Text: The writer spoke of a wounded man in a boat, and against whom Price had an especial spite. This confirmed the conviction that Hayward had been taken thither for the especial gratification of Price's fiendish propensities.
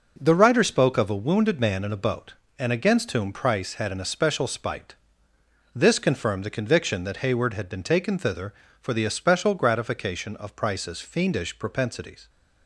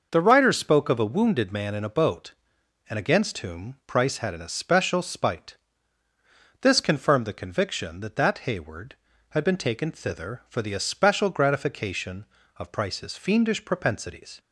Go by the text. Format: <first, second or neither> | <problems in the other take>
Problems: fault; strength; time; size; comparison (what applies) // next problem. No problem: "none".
first | says "that" twice; at 8.1 s